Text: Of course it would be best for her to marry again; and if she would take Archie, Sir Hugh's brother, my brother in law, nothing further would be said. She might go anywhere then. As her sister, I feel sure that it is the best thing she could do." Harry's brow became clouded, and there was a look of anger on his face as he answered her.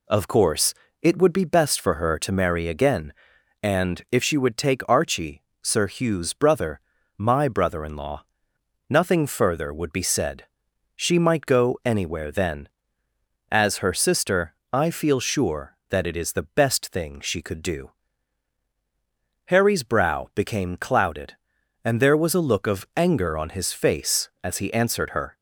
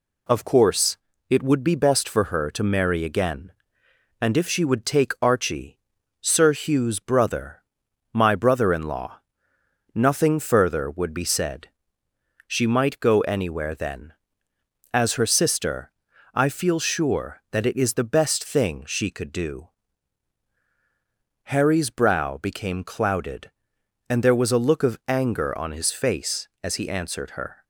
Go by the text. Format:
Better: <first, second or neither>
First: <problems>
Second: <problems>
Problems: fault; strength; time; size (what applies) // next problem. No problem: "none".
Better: neither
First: pauses between "course" and "it"; slight; at 0.7 s; 0.28 s long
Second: pauses between "course" and "it"; slight; at 0.9 s; 0.32 s long